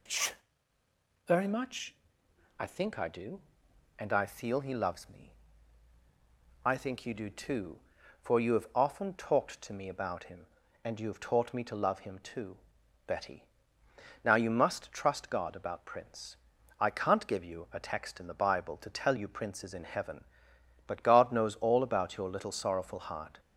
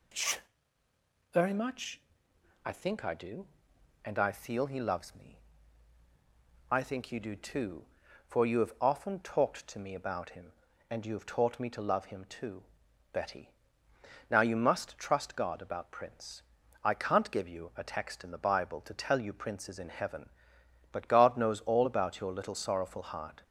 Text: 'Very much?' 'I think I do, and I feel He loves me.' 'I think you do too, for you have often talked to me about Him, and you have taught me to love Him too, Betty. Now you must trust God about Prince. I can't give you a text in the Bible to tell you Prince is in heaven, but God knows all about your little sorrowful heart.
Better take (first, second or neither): neither